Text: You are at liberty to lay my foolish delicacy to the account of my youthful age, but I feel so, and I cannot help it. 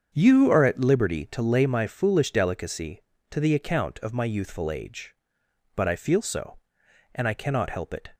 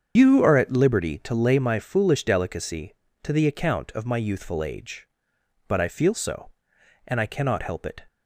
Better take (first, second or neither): first